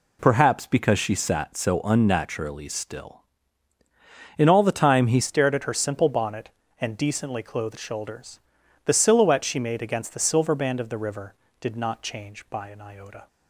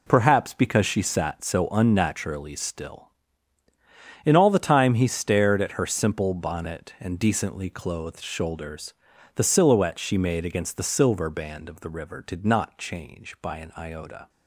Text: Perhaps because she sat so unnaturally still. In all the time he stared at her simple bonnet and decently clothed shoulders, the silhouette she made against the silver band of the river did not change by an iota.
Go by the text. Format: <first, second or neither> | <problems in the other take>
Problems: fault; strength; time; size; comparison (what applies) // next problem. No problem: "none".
second | changes voice at "stared"; from 5.2 s on; 8.0 s long